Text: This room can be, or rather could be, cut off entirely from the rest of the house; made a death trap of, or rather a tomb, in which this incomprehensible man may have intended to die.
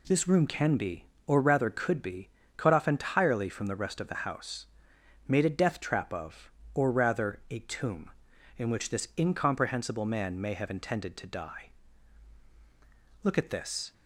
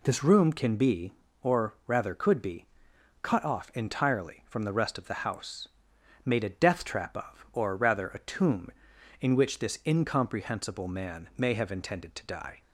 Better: second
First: goes on to say "Look at this"; noticeable; from 13.2 s on; 0.70 s long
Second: none

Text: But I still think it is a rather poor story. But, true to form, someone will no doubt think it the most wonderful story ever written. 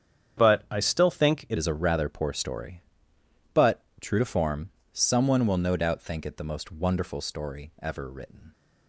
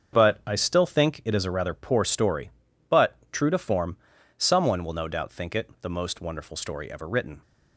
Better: second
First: starts louder than the rest; strong; until 1.4 s; 8.5 dB // changes voice at "is"; from 1.5 s on; 7.0 s long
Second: starts louder than the rest; strong; until 1.2 s; 7 dB

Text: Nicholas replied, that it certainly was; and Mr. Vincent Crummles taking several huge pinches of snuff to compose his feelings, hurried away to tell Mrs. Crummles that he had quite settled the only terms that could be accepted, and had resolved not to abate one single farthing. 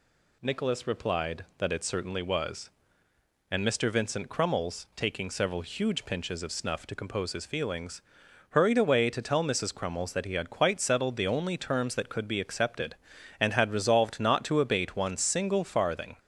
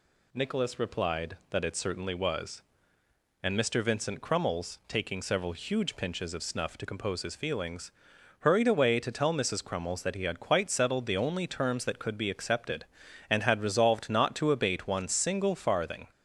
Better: neither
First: none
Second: none

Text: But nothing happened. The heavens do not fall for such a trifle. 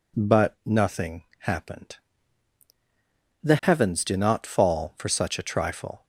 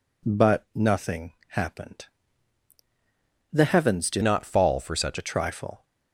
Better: first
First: pauses between "nothing" and "happened"; slight; at 1.2 s; 0.16 s long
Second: pauses between "nothing" and "happened"; slight; at 1.3 s; 0.16 s long // changes voice from "not" to "such"; from 4.2 to 5.1 s; 0.9 s long

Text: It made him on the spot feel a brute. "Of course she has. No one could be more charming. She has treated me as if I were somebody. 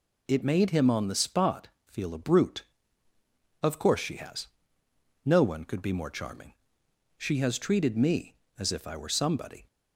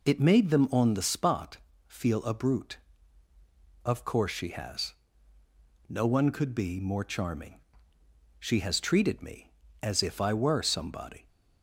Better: first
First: pauses between "spot" and "feel"; slight; at 1.6 s; 0.18 s long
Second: says "them" for "him"; at 0.4 s // pauses between "spot" and "feel"; slight; at 1.5 s; 0.30 s long

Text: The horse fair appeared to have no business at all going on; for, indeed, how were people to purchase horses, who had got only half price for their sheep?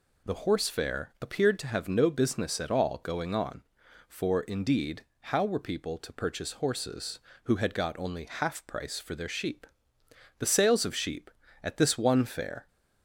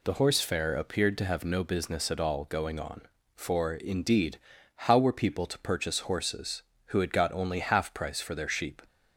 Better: second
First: goes on to say "The sales of sheep at this one fair"; strong; from 10.3 s on; 2.3 s long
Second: none

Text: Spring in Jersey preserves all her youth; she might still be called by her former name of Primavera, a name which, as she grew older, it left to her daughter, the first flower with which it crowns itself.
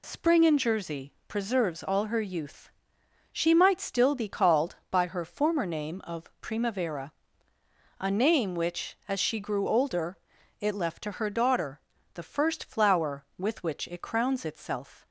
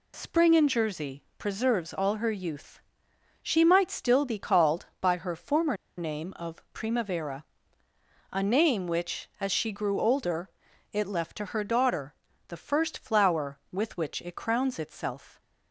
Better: first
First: none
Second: pauses between "former" and "name"; slight; at 5.7 s; 0.22 s long

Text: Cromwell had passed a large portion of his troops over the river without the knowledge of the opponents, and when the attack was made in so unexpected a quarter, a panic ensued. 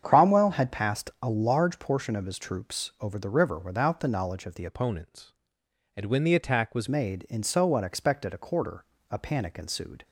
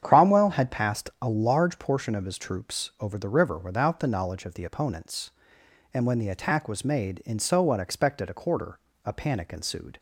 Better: second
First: starts louder than the rest; strong; until 1.0 s; 8 dB // changes voice from "opponents" to "was"; from 4.6 to 6.8 s; 2.2 s long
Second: starts louder than the rest; strong; until 1.0 s; 8.5 dB

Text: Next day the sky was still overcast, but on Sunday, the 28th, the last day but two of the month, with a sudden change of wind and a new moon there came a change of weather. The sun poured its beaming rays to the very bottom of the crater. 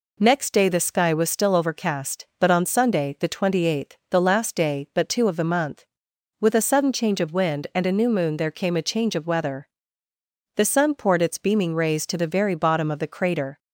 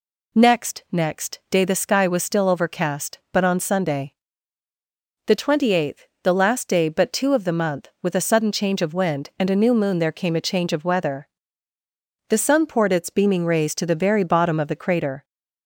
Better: first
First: none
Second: says "Next" twice; at 0.9 s

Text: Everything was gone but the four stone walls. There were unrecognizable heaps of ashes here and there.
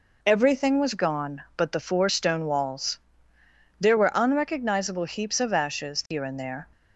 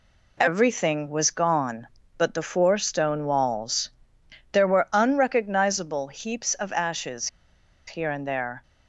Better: first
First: none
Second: pauses between "ashes" and "here"; noticeable; at 7.2 s; 0.60 s long

